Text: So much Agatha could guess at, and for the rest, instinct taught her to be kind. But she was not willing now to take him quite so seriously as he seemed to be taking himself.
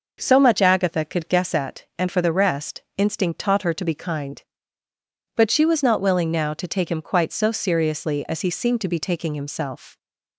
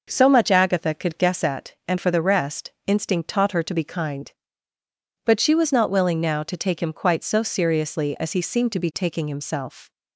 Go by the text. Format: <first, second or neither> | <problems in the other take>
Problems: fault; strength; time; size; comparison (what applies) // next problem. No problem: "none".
neither | none